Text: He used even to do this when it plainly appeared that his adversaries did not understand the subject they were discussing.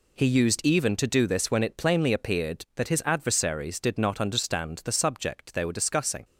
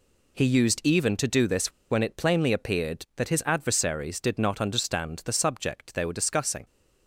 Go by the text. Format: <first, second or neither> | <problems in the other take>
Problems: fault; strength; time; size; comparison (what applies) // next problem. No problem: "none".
first | pauses between "this" and "when"; slight; at 1.7 s; 0.19 s long